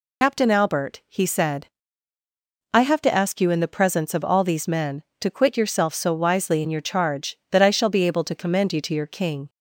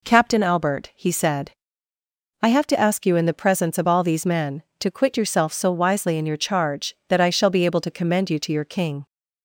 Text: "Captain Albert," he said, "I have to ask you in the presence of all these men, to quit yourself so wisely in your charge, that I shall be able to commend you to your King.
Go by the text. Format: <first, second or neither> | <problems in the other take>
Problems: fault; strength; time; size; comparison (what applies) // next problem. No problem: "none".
second | loses the start of "Captain"; at 0.2 s; 100 ms